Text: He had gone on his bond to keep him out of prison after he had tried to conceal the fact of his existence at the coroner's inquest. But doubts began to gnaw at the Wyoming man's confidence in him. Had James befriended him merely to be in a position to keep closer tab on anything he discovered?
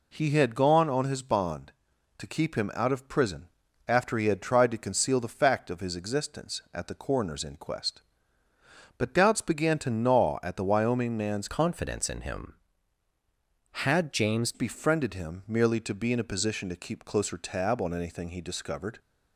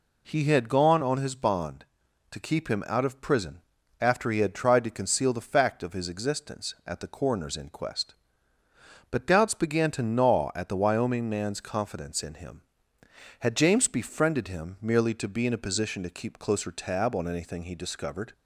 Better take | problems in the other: second | pauses between "prison" and "after"; at 3.4 s; 0.40 s long; also in the second // changes voice from "confidence" to "James"; from 11.4 to 14.5 s; 3.1 s long

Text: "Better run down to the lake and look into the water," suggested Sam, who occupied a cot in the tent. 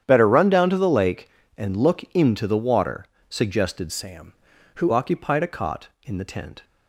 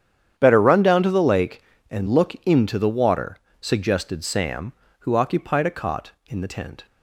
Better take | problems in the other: second | starts louder than the rest; strong; until 1.0 s; 9.5 dB; strong in the second // changes voice from "Sam" to "who"; from 3.9 to 4.9 s; 1.0 s long

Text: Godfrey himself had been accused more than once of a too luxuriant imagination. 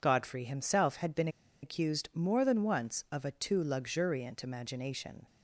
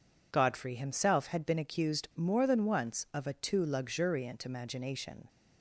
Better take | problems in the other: second | pauses between "been" and "accused"; slight; at 1.2 s; 0.34 s long

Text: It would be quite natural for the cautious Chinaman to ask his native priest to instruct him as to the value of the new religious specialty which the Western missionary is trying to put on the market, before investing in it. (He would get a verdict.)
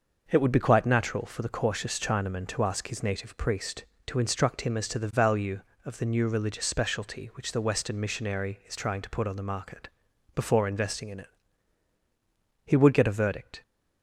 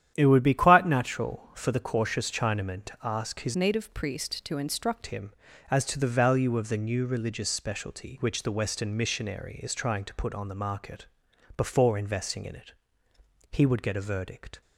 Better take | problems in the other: first | starts louder than the rest; strong; until 1.1 s; 10 dB; noticeable in the first // changes voice from "native" to "instruct"; from 3.5 to 5.0 s; 1.5 s long

